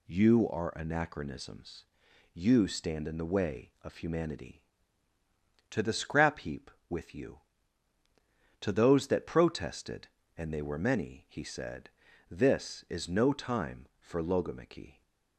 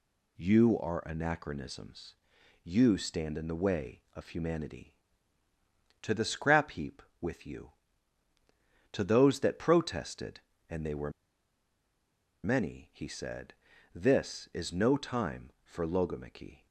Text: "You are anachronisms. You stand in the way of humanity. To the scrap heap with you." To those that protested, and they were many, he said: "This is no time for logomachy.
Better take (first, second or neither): first